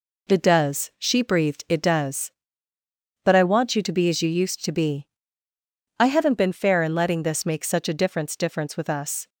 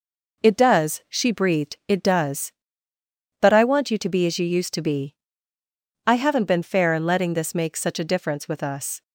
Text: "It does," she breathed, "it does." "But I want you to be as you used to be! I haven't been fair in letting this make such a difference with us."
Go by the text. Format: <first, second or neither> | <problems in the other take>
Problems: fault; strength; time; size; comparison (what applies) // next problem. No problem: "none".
second | says "difference" twice; at 8.3 s